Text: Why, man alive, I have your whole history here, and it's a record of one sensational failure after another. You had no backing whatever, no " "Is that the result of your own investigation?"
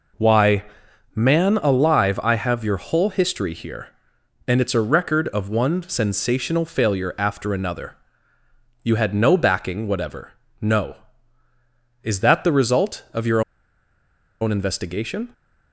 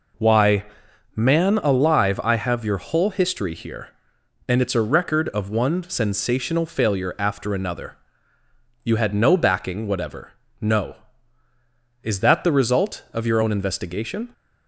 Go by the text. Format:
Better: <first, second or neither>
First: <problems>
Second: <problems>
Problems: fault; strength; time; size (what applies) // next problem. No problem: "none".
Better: second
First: pauses between "your" and "own"; at 13.4 s; 1.0 s long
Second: none